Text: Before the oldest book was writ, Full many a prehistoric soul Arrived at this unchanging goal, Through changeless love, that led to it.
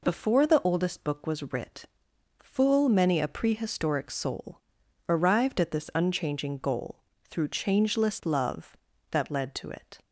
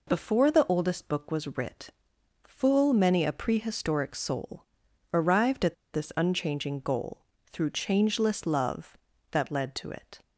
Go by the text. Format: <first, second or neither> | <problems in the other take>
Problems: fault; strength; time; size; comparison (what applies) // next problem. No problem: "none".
first | pauses between "soul" and "Arrived"; noticeable; at 4.6 s; 0.48 s long; noticeable in the first // pauses between "at" and "this"; slight; at 5.7 s; 0.18 s long